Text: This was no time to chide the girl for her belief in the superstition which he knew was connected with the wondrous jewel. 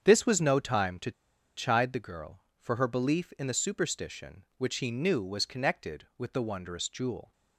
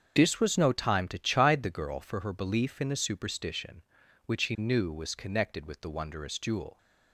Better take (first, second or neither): second